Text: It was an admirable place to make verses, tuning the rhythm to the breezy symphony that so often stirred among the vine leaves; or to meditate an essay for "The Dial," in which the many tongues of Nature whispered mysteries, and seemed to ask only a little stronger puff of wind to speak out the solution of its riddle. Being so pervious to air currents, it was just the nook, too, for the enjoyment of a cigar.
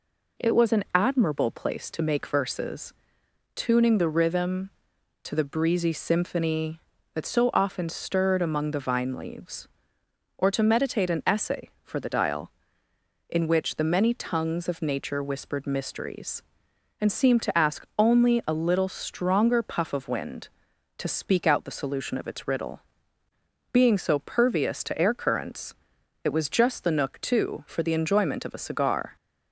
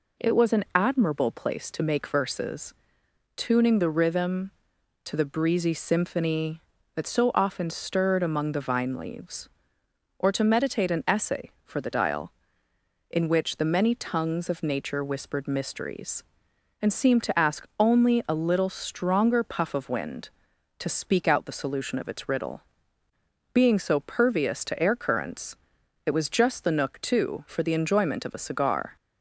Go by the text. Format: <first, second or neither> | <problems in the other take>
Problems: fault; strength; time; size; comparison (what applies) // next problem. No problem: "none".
neither | none